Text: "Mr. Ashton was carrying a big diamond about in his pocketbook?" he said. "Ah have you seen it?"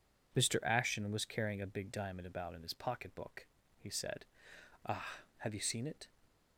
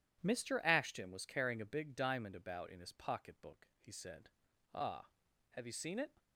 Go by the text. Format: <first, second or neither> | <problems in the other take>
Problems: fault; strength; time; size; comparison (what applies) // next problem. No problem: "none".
neither | none